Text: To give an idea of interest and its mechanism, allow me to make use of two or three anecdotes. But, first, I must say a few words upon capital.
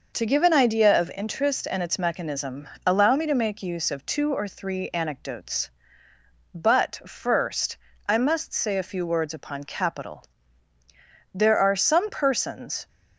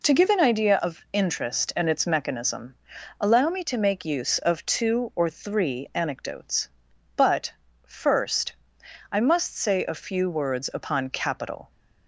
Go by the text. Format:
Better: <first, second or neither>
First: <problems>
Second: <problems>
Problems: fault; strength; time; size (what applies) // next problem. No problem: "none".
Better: second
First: goes on to say "There are some persons"; from 11.3 s on; 1.5 s long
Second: none